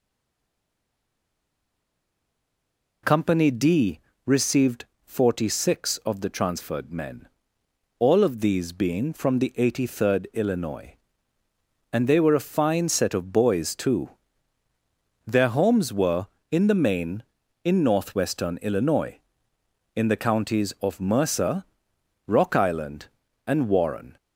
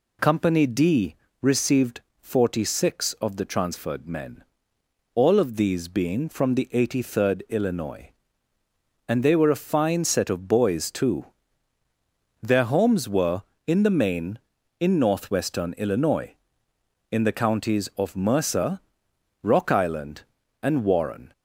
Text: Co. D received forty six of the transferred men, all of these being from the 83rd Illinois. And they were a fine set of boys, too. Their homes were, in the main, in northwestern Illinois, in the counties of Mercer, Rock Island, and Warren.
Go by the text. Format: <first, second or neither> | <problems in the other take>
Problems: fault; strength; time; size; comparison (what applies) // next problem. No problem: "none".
second | stays silent before the first word; strong; until 3.0 s; 3.0 s long // pauses between "D" and "received"; slight; at 4.0 s; 0.24 s long; slight in the second // pauses between "received" and "forty"; slight; at 4.8 s; 0.18 s long; slight in the second